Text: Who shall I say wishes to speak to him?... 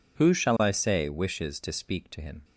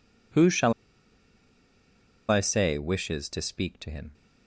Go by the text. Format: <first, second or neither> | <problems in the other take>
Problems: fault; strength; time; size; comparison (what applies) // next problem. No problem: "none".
first | pauses between "shall" and "I"; strong; at 0.7 s; 1.5 s long